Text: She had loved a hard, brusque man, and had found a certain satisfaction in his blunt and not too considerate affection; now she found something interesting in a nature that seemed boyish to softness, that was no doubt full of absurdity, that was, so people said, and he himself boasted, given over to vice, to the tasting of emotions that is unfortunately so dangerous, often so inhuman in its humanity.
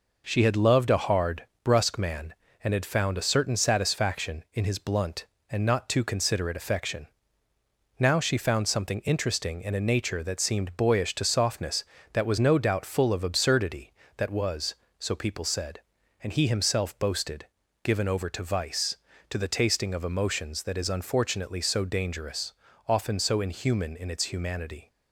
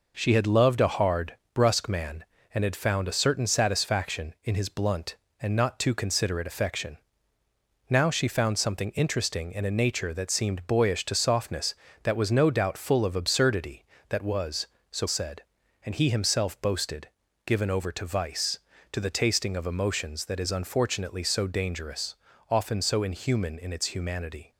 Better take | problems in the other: first | skips "people"; at 15.0 s

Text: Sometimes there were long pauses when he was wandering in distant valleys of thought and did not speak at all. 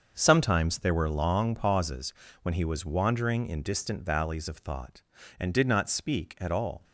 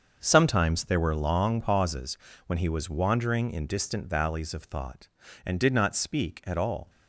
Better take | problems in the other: neither | starts louder than the rest; the same in both // pauses between "pauses" and "when"; slight; the same in both

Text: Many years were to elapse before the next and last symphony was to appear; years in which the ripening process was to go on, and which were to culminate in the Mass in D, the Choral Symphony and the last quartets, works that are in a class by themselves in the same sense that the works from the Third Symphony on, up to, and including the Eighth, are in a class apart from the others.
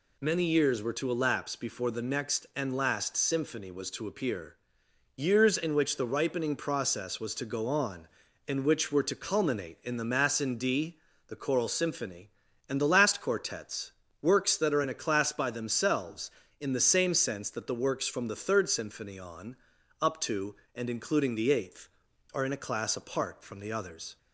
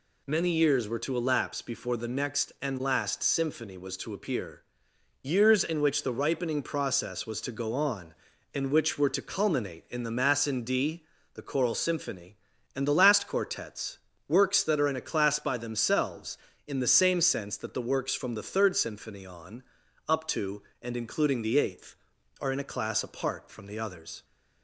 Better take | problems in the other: neither | none

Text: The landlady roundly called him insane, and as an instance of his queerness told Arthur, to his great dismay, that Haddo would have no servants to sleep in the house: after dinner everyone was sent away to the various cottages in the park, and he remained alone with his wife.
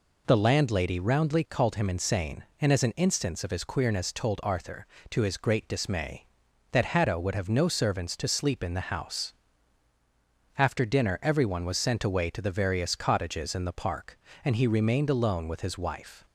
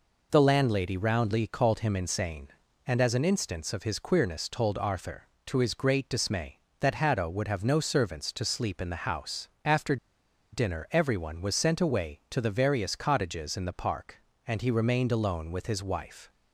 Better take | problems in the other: first | pauses between "after" and "dinner"; noticeable; at 9.9 s; 0.56 s long

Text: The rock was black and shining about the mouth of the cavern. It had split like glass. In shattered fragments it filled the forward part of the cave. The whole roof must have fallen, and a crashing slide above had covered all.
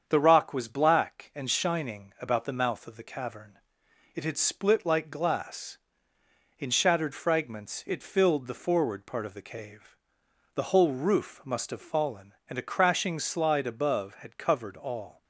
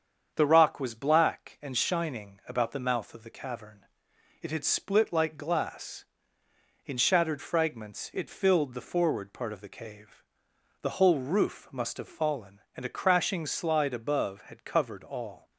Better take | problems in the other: neither | starts louder than the rest; strong; the same in both

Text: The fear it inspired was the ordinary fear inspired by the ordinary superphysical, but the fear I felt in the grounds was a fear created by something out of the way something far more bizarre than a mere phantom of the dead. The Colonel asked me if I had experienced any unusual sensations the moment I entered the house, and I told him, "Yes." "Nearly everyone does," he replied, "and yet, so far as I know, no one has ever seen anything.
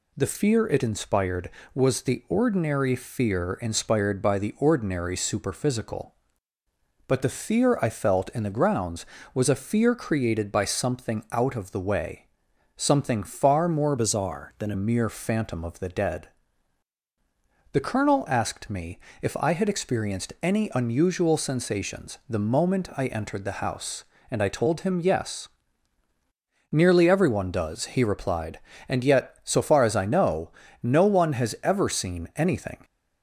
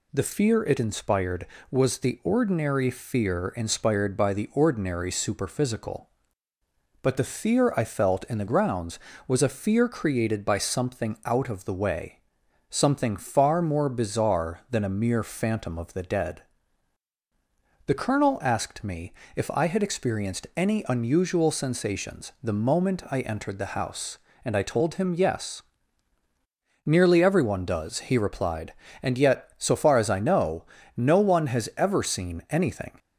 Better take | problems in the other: second | pauses between "way" and "something"; noticeable; at 12.2 s; 0.48 s long; noticeable in the second // changes voice from "bizarre" to "a"; from 13.9 to 14.7 s; 0.8 s long // pauses between "me" and "if"; slight; at 19.0 s; 0.22 s long; slight in the second

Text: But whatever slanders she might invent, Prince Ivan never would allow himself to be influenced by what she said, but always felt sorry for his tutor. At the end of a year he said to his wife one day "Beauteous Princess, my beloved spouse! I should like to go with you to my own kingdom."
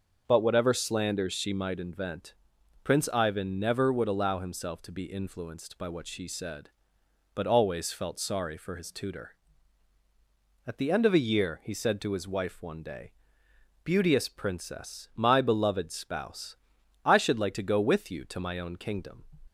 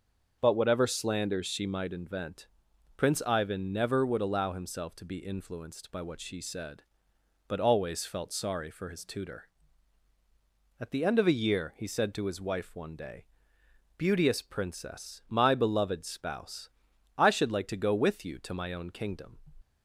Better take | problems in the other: neither | starts louder than the rest; the same in both // pauses between "day" and "Beauteous"; noticeable; the same in both

